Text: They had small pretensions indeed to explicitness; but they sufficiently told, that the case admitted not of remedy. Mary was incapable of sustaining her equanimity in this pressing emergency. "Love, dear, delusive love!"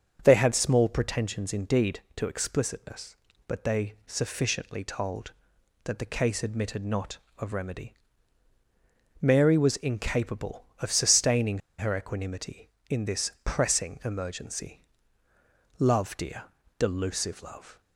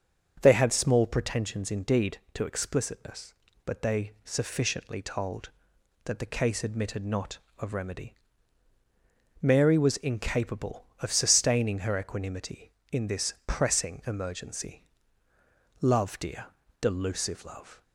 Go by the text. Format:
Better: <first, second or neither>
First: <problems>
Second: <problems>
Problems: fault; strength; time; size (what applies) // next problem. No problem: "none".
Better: second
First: starts louder than the rest; strong; until 1.2 s; 7 dB // pauses between "sustaining" and "her"; slight; at 11.6 s; 0.18 s long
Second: starts louder than the rest; strong; until 1.4 s; 7 dB